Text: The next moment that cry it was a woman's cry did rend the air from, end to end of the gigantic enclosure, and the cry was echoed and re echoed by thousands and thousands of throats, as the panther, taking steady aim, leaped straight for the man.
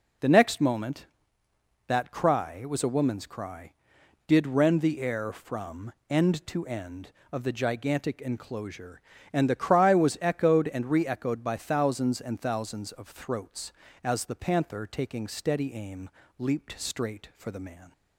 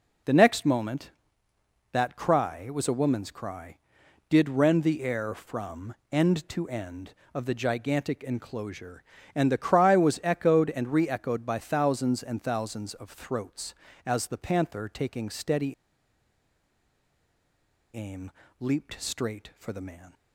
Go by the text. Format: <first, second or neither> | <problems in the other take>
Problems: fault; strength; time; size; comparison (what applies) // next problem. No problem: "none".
first | pauses between "steady" and "aim"; strong; at 15.7 s; 2.1 s long